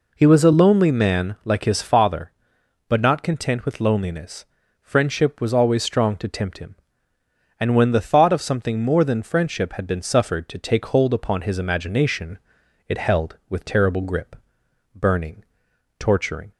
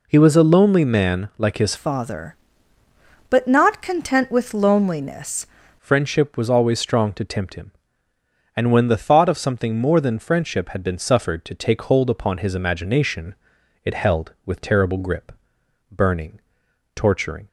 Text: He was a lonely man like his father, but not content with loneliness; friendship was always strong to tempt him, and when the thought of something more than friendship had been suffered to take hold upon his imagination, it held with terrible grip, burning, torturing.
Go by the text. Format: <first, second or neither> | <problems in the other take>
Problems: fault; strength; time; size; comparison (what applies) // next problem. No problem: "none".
first | changes voice from "father" to "loneliness"; from 1.7 to 5.4 s; 3.7 s long